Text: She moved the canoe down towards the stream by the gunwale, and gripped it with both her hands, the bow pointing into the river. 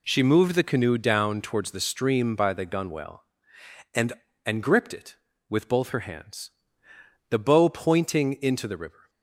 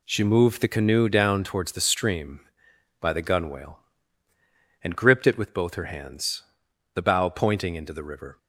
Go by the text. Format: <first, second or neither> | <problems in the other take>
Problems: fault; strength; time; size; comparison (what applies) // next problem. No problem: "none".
second | says "and" twice; at 4.4 s